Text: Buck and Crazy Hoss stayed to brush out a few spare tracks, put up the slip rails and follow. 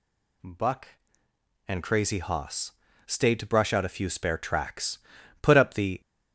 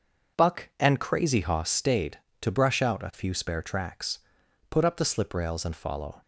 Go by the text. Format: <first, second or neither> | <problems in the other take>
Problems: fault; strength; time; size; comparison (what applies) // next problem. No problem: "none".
second | pauses between "Hoss" and "stayed"; slight; at 2.7 s; 0.34 s long // stops before "slip rails and follow"; at 6.0 s